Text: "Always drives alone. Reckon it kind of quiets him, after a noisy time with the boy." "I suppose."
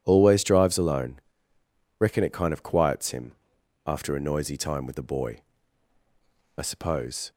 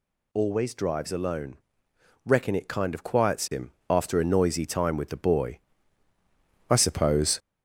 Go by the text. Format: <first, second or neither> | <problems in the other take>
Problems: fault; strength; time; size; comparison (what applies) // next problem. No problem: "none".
first | gets louder; noticeable; throughout; 4 dB